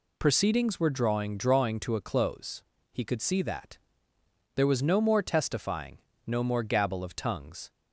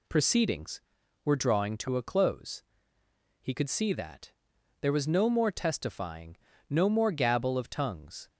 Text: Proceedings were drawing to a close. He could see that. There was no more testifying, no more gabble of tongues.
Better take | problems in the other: second | says "drawing" twice; at 1.3 s

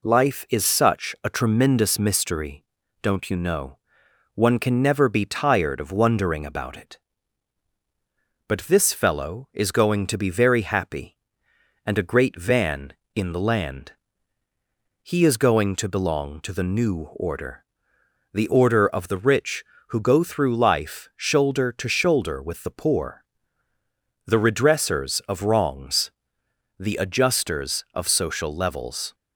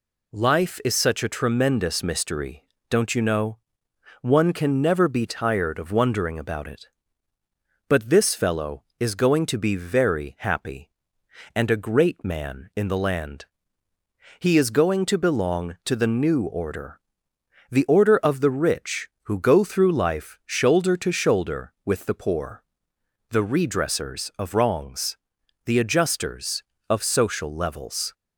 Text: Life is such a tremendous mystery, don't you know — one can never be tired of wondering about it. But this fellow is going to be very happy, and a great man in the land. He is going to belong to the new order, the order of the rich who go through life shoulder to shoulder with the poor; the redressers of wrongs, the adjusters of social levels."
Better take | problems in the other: second | says "van" for "man"; at 12.3 s

